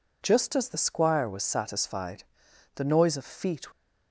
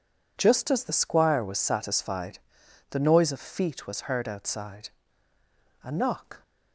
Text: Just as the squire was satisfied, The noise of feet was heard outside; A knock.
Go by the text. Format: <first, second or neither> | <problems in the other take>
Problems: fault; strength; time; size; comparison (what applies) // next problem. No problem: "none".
second | stops before "was heard outside A knock"; at 3.7 s